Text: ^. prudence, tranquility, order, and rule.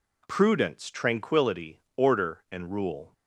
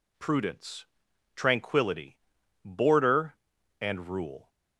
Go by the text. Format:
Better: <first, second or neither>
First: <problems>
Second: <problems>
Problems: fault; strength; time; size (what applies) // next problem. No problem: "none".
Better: first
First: none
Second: says "border" for "order"; at 2.6 s